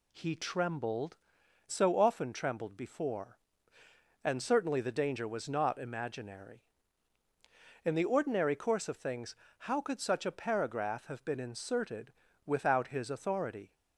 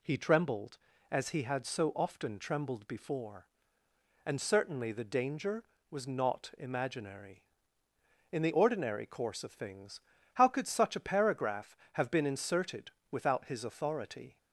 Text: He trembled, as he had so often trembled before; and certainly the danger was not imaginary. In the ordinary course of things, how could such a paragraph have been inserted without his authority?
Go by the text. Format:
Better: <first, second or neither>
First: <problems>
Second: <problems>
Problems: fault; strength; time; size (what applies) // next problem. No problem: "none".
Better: second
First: skips "as he had"; at 1.4 s // pauses between "inserted" and "without"; slight; at 12.1 s; 0.32 s long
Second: pauses between "inserted" and "without"; slight; at 12.9 s; 0.18 s long